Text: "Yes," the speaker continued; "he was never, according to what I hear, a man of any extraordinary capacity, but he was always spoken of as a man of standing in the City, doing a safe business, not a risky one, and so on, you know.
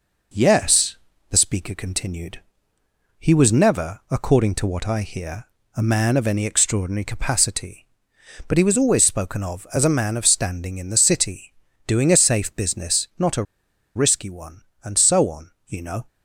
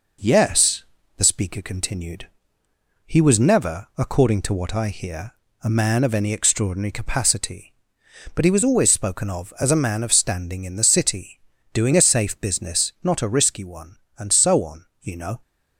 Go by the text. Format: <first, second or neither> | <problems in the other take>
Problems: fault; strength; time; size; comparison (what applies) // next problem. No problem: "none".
second | pauses between "a" and "risky"; noticeable; at 13.4 s; 0.53 s long